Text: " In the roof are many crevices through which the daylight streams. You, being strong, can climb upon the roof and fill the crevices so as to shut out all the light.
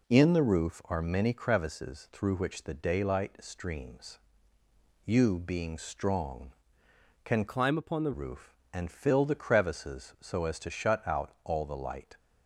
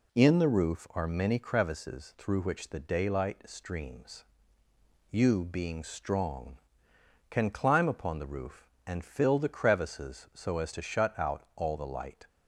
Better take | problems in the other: second | changes voice from "climb" to "the"; from 7.4 to 8.1 s; 0.7 s long

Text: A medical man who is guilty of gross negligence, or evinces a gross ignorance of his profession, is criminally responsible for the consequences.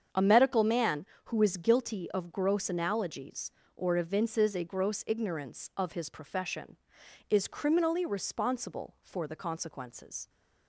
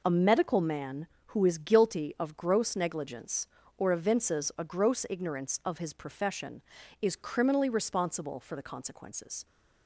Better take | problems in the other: second | starts louder than the rest; strong; until 1.3 s; 7.5 dB // says "analogies" for "negligence"; at 2.6 s

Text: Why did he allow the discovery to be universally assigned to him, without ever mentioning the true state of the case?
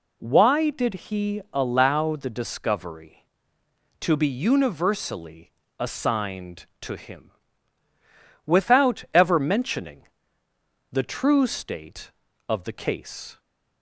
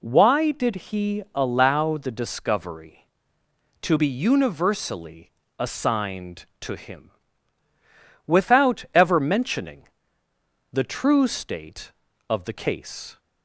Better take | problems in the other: neither | pauses between "universally" and "assigned"; slight; the same in both // pauses between "mentioning" and "the"; noticeable; the same in both

